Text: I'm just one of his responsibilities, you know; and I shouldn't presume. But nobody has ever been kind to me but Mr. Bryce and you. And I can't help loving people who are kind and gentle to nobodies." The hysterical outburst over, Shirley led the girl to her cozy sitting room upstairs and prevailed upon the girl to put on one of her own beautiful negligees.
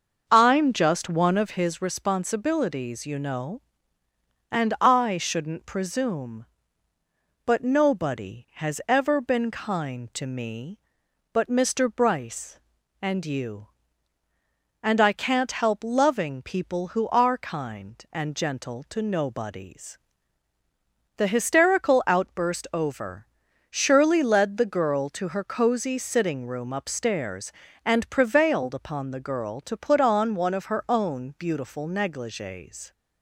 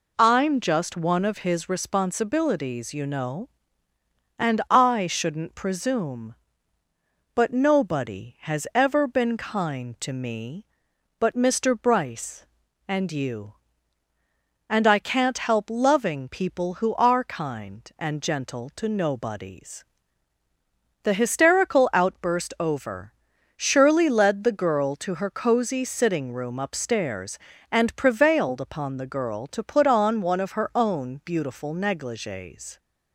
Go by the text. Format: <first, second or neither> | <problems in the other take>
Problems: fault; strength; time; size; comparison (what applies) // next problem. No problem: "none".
second | starts louder than the rest; until 1.7 s; 6.5 dB